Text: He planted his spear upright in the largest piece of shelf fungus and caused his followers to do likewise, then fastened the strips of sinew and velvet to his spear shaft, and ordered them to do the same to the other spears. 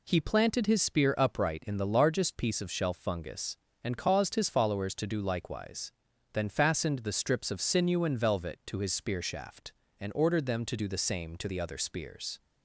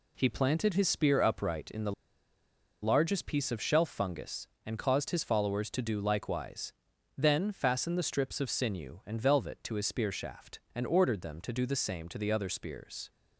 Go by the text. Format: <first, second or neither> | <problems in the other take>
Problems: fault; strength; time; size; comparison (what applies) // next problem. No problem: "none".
first | pauses between "the" and "largest"; noticeable; at 1.9 s; 0.90 s long